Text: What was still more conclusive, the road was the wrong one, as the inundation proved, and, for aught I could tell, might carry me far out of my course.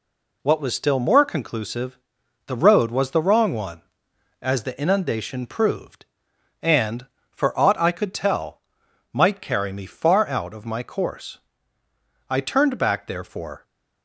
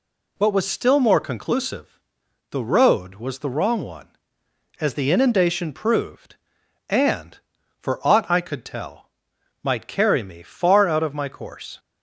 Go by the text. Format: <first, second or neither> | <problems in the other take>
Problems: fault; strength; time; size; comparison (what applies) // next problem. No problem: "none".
second | goes on to say "I turned back therefore"; from 12.2 s on; 1.3 s long